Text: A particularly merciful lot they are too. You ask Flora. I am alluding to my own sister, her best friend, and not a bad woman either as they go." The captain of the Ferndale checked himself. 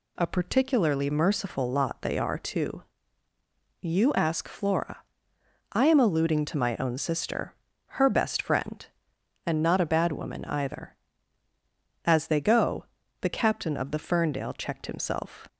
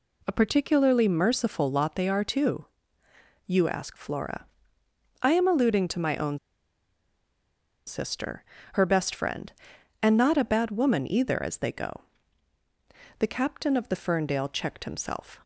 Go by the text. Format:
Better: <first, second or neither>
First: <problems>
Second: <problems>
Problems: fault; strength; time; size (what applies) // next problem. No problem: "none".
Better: first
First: none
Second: pauses between "own" and "sister"; strong; at 6.3 s; 1.4 s long